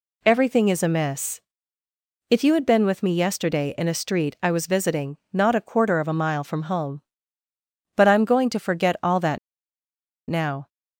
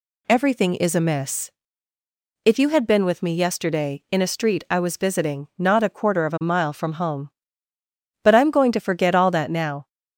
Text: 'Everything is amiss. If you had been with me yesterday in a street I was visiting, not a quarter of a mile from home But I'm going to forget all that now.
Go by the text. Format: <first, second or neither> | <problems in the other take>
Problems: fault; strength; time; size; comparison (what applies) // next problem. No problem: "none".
second | pauses between "that" and "now"; noticeable; at 9.3 s; 0.92 s long